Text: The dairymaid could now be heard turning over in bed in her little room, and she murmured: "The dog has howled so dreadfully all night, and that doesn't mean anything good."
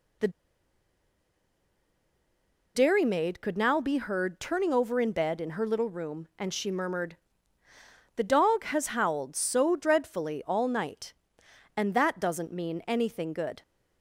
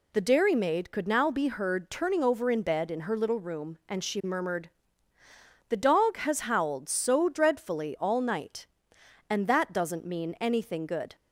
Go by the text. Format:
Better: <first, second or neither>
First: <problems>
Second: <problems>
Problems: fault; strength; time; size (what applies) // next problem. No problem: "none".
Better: second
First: pauses between "The" and "dairymaid"; strong; at 0.2 s; 2.4 s long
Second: none